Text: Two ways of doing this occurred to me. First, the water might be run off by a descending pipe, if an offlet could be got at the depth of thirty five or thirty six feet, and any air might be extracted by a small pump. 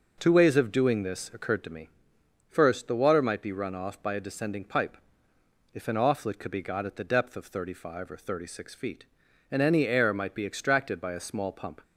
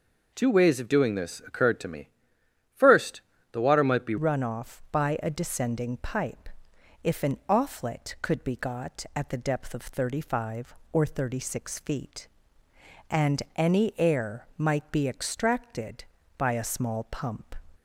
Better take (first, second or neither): first